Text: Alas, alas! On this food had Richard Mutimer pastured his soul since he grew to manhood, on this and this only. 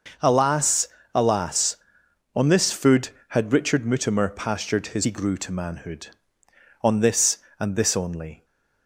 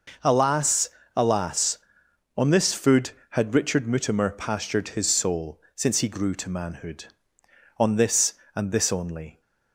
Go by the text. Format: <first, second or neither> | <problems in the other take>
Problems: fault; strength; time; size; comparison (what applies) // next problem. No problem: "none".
second | skips "soul since"; at 5.0 s